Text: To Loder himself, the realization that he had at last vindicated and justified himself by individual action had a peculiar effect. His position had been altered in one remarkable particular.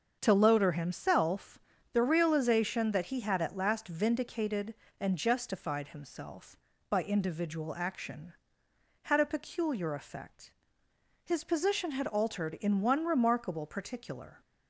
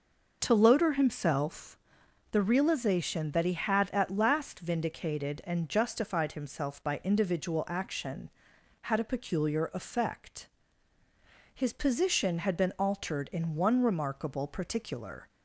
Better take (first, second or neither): second